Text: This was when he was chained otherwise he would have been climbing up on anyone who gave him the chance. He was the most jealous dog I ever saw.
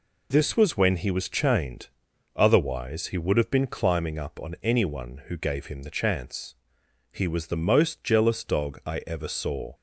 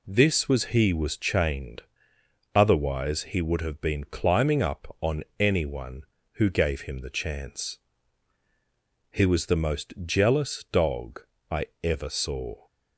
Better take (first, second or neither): first